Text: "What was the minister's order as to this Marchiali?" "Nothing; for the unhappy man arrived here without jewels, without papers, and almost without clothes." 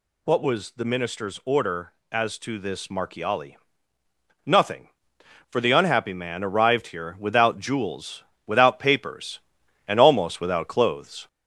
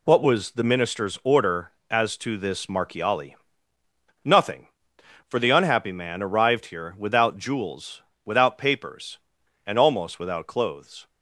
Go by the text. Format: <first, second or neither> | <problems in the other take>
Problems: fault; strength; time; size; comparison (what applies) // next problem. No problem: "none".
second | gets louder; slight; throughout; 2.5 dB